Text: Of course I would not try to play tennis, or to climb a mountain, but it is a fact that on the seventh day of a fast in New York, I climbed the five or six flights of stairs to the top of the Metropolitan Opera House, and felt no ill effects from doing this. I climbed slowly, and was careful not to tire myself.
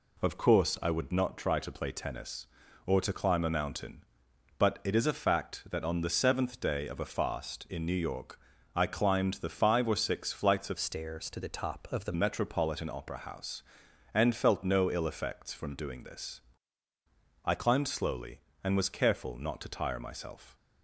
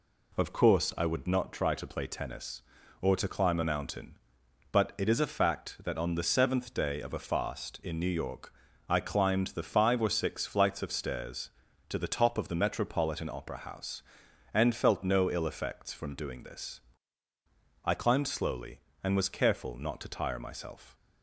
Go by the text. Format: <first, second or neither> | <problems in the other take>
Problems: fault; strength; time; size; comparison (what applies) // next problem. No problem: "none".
second | changes voice from "stairs" to "the"; from 10.7 to 12.1 s; 1.4 s long